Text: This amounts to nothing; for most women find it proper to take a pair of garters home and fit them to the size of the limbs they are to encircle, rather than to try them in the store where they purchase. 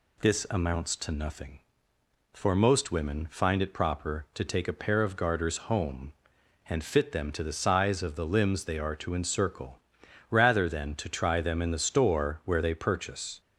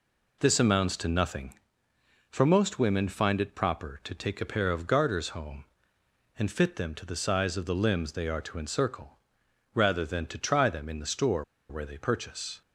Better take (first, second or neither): first